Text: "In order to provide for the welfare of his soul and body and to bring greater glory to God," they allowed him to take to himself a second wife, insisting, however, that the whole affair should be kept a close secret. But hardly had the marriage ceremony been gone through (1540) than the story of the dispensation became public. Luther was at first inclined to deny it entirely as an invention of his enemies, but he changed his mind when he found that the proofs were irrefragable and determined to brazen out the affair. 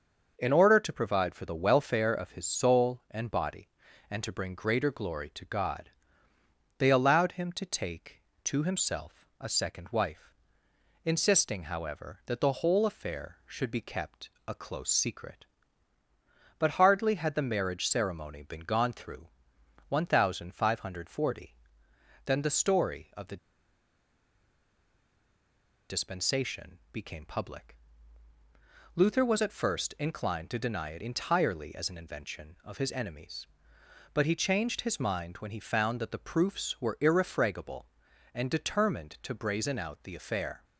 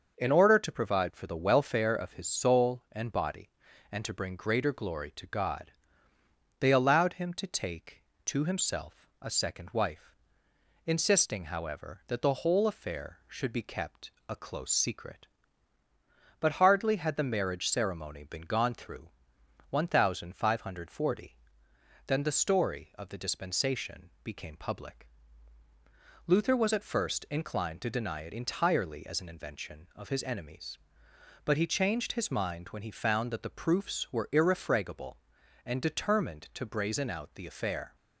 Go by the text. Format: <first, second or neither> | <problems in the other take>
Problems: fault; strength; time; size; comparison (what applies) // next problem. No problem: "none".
second | starts louder than the rest; until 1.3 s; 6.5 dB; also in the second // pauses between "kept" and "a"; slight; at 14.2 s; 0.16 s long; slight in the second // pauses between "the" and "dispensation"; strong; at 23.3 s; 2.5 s long